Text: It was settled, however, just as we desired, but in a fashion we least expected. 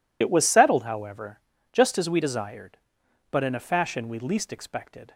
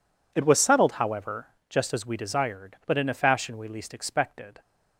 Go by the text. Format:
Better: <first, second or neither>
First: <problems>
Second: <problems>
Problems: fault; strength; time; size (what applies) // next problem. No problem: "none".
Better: second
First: loses the start of "It"; at 0.2 s; 65 ms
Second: none